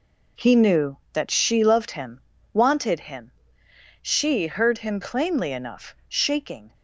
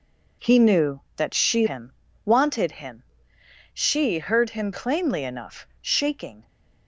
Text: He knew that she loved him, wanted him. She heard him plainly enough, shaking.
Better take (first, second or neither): first